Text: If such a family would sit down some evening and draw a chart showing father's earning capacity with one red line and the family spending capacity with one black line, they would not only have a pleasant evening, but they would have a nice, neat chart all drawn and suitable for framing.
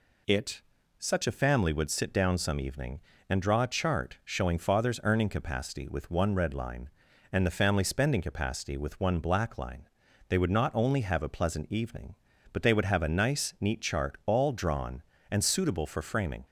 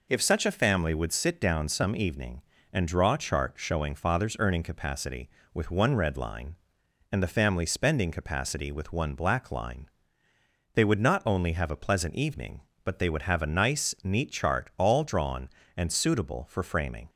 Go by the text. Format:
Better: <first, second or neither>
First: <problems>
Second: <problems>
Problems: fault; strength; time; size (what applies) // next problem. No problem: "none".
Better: second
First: says "It" for "If"; at 0.2 s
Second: none